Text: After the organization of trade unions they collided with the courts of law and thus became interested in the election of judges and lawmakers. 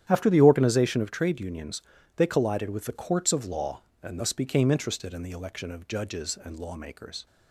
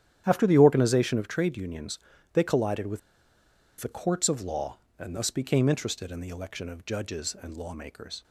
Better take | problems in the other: first | starts louder than the rest; strong; until 1.2 s; 10.5 dB; strong in the first // pauses between "unions" and "they"; slight; at 1.9 s; 0.36 s long; slight in the first // pauses between "with" and "the"; noticeable; at 2.9 s; 0.81 s long

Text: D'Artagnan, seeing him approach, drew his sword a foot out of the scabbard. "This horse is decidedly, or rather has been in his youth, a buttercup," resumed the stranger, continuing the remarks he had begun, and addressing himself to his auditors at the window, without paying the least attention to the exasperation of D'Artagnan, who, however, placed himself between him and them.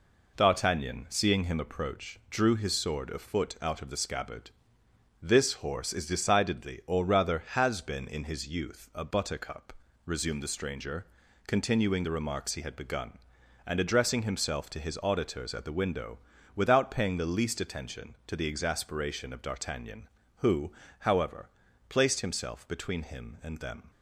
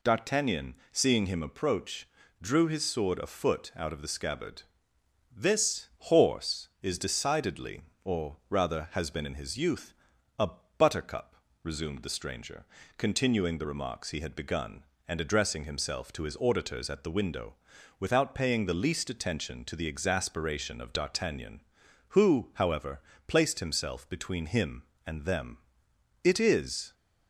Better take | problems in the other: first | pauses between "a" and "buttercup"; slight; at 10.5 s; 0.26 s long // goes on to say "It is"; noticeable; from 26.2 s on; 0.70 s long

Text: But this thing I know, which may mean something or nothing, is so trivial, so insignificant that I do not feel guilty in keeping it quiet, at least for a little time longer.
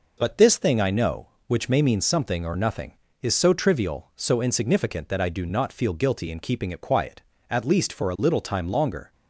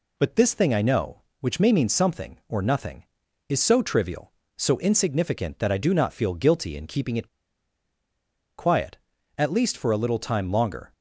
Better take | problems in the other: first | pauses between "it" and "quiet"; strong; at 7.2 s; 1.3 s long

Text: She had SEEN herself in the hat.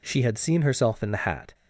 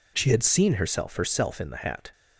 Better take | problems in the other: first | says "herself" twice; at 1.1 s

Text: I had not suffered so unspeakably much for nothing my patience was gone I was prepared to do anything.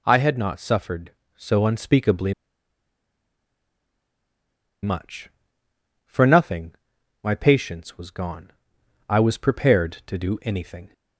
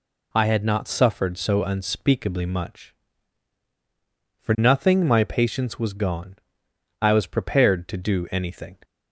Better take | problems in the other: second | pauses between "unspeakably" and "much"; strong; at 2.3 s; 2.4 s long // pauses between "nothing" and "my"; noticeable; at 6.7 s; 0.48 s long // pauses between "gone" and "I"; noticeable; at 8.5 s; 0.56 s long; noticeable in the second

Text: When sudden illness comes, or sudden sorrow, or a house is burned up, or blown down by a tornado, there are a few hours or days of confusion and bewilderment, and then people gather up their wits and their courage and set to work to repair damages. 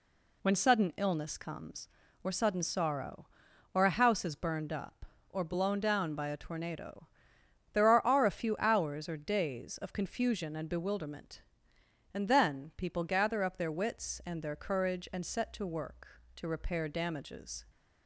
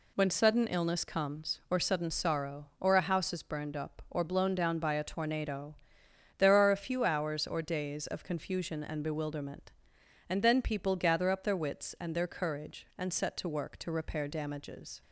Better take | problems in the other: second | says "are" twice; at 8.0 s

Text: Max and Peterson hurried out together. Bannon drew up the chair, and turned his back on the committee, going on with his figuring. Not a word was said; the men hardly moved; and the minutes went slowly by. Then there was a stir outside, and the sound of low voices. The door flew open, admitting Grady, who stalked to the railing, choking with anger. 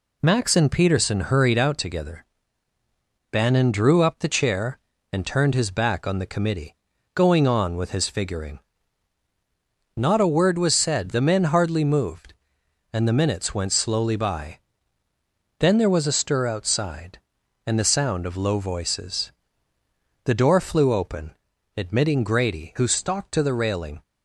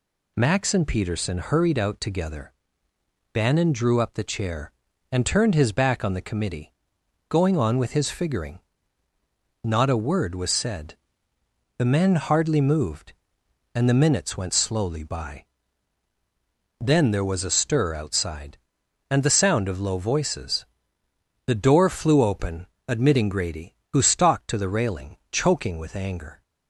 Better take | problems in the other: second | stops before "choking with anger"; at 24.0 s

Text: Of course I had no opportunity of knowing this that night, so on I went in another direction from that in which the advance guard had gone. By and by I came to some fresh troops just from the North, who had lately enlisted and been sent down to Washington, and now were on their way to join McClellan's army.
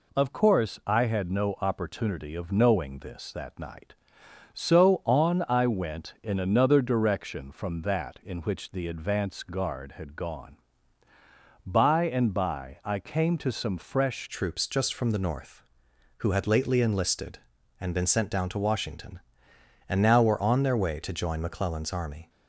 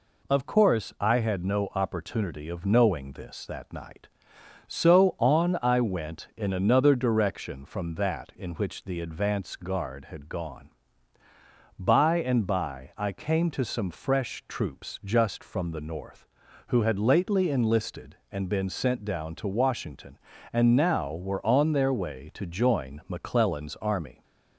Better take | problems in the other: second | changes voice at "troops"; from 14.2 s on; 8.0 s long

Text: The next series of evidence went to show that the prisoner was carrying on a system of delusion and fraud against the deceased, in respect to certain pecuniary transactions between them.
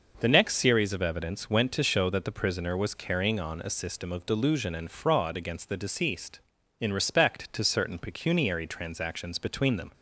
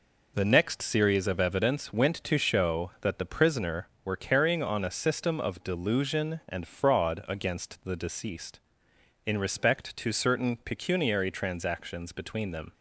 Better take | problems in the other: first | says "were" for "was"; at 4.0 s

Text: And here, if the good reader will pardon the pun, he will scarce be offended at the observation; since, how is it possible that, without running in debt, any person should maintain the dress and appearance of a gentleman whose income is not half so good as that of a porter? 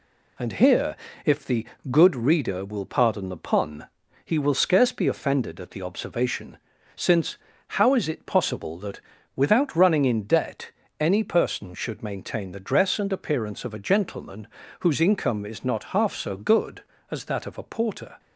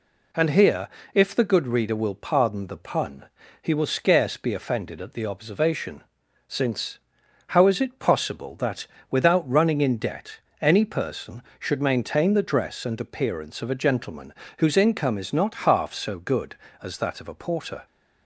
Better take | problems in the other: second | gets quieter; throughout; 4 dB // pauses between "the" and "good"; slight; at 1.6 s; 0.24 s long // pauses between "gentleman" and "whose"; slight; at 14.4 s; 0.32 s long; slight in the second

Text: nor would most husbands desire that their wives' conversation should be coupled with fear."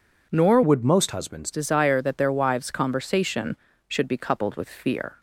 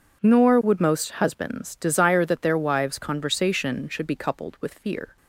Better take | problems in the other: second | changes voice from "would" to "husbands"; from 0.6 to 1.4 s; 0.8 s long

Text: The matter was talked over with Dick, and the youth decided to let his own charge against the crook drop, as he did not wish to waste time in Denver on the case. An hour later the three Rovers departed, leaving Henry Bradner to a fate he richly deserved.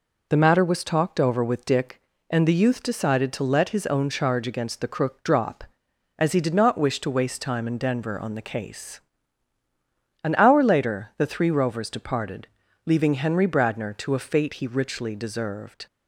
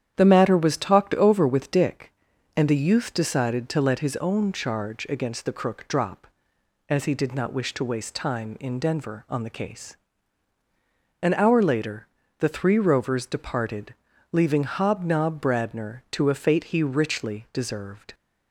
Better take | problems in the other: first | starts louder than the rest; strong; until 1.1 s; 9.5 dB // pauses between "later" and "the"; slight; at 12.0 s; 0.34 s long // says "Hobnob" for "Henry"; at 14.6 s

